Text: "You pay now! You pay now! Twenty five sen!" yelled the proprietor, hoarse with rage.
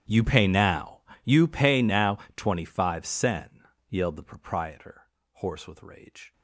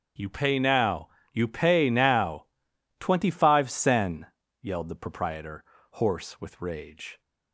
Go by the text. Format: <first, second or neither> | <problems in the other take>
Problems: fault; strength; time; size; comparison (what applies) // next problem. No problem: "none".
second | gets quieter; strong; throughout; 25.5 dB // starts louder than the rest; strong; until 1.3 s; 10.5 dB; strong in the second